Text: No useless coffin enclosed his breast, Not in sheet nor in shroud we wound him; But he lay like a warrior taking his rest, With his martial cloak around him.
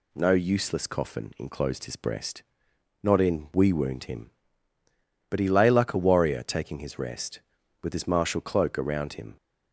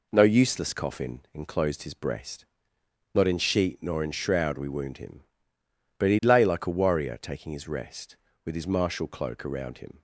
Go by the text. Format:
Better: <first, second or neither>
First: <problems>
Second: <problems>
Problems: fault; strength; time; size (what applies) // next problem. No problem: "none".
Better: second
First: skips "sheet nor in shroud"; at 3.5 s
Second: none